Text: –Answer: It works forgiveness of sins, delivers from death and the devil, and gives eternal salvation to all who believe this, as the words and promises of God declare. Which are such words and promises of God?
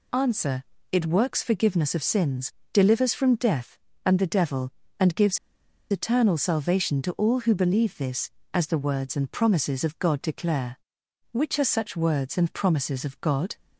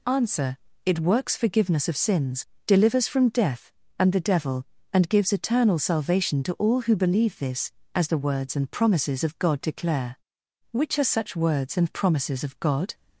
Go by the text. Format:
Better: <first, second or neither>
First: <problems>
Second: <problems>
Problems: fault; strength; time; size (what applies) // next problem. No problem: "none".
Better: second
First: pauses between "gives" and "eternal"; noticeable; at 5.3 s; 0.53 s long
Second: none